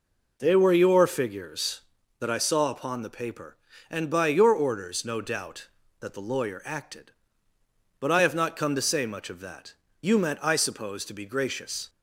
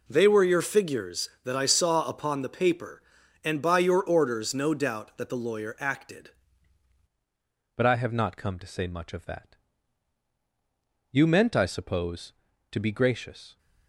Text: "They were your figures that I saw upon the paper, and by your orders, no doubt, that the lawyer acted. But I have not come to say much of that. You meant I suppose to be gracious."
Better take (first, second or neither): first